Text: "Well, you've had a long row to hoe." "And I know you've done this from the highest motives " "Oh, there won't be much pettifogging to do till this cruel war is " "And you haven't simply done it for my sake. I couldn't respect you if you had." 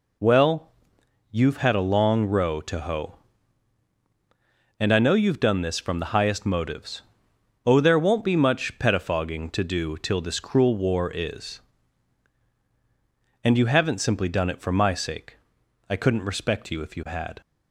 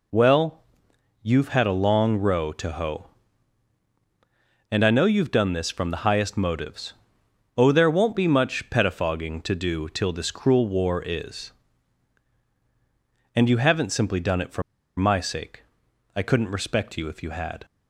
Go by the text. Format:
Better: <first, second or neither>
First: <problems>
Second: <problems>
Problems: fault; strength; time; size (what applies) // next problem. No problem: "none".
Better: first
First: none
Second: pauses between "for" and "my"; at 14.6 s; 0.36 s long